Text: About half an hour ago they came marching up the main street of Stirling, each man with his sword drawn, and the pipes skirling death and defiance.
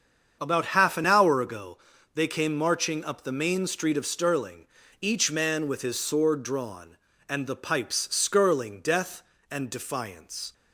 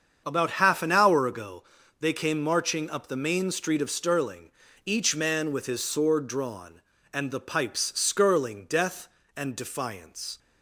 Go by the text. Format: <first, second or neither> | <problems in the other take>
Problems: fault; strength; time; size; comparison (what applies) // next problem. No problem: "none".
neither | starts louder than the rest; strong; the same in both // pauses between "ago" and "they"; slight; the same in both